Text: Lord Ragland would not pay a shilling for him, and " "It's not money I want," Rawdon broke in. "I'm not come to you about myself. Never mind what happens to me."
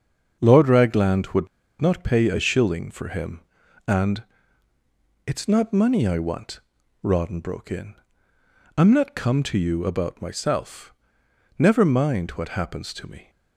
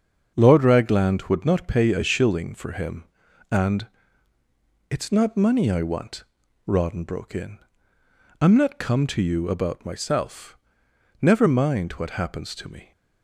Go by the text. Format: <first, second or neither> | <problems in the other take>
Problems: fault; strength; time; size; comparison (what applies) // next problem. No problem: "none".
second | starts louder than the rest; strong; until 1.4 s; 8 dB; strong in the second // pauses between "would" and "not"; slight; at 1.4 s; 0.34 s long